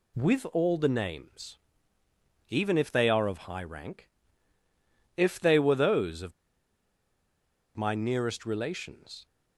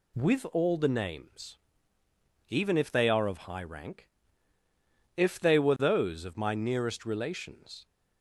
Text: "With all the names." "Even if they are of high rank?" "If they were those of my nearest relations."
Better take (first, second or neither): second